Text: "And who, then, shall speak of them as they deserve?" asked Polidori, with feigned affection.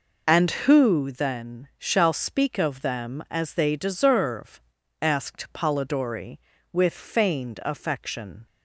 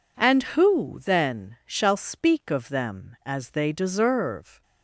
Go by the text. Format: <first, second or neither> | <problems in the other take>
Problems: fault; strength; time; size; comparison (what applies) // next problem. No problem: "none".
first | stops before "asked Polidori with feigned affection"; at 4.6 s